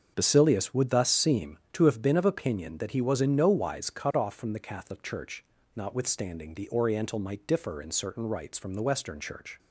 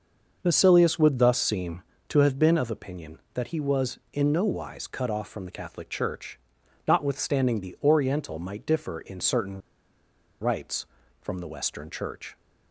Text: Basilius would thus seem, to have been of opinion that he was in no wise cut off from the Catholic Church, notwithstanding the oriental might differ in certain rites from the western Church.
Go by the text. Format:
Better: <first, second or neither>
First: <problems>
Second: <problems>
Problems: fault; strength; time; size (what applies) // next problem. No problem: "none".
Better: first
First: starts louder than the rest; until 1.1 s; 7 dB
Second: starts louder than the rest; until 1.4 s; 6 dB // pauses between "certain" and "rites"; noticeable; at 9.5 s; 0.81 s long